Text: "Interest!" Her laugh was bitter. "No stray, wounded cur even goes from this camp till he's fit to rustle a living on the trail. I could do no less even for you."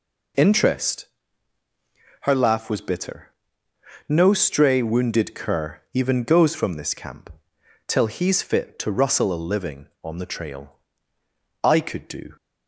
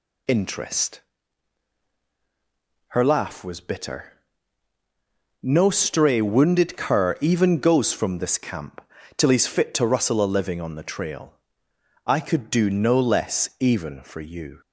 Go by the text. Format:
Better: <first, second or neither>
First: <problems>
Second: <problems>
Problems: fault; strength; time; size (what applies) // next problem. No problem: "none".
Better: second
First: pauses between "camp" and "till"; noticeable; at 7.3 s; 0.56 s long // stops before "no less even for you"; at 12.3 s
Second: pauses between "camp" and "till"; slight; at 8.8 s; 0.36 s long